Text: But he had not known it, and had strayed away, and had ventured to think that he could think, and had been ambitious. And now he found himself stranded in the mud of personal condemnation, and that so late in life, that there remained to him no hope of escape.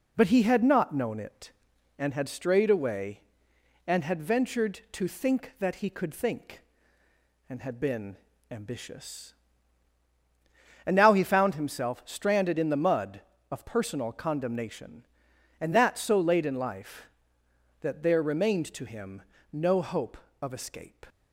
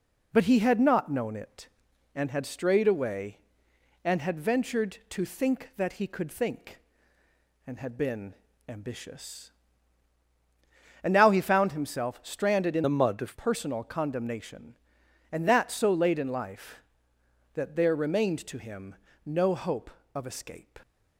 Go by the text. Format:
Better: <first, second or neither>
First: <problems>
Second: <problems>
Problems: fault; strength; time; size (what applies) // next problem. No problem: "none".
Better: first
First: pauses between "been" and "ambitious"; slight; at 8.1 s; 0.34 s long // pauses between "him" and "no"; slight; at 19.2 s; 0.30 s long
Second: pauses between "been" and "ambitious"; slight; at 8.3 s; 0.34 s long // changes voice from "the" to "of"; from 12.8 to 13.3 s; 0.5 s long // pauses between "him" and "no"; slight; at 18.9 s; 0.30 s long